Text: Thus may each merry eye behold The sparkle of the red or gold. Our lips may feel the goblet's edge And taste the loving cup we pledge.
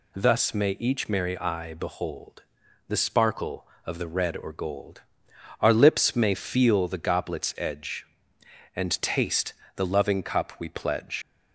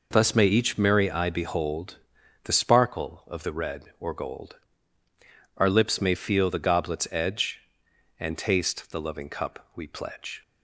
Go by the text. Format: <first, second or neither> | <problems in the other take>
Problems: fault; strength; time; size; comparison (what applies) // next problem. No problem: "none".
second | pauses between "behold" and "The"; noticeable; at 2.4 s; 0.46 s long; noticeable in the second // pauses between "taste" and "the"; slight; at 9.5 s; 0.24 s long // leaves "pledge" unfinished; at 11.2 s; 90 ms